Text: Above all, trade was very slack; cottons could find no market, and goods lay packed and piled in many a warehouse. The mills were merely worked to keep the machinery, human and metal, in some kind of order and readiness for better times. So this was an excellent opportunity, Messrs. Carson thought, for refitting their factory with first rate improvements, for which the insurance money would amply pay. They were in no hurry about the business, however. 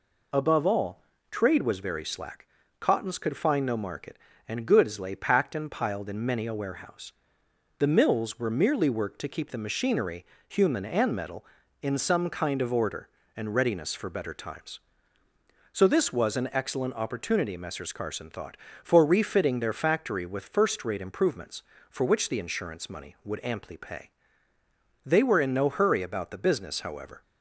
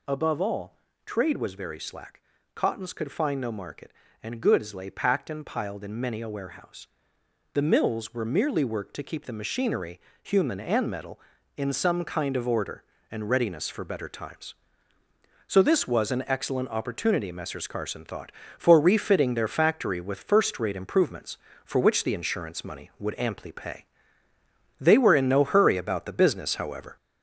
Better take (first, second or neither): first